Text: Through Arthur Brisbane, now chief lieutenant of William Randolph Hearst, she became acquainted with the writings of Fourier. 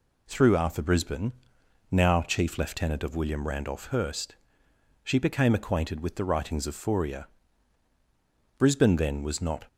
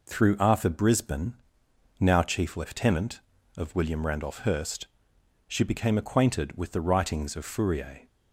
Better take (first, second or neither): second